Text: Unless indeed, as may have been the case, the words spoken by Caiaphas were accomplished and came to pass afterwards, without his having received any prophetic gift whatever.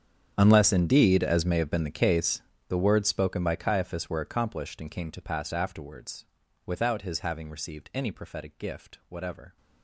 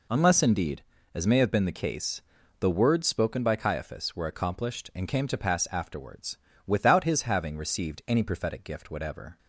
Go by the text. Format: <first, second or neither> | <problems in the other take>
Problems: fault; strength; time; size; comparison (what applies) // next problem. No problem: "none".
second | gets quieter; strong; throughout; 19.5 dB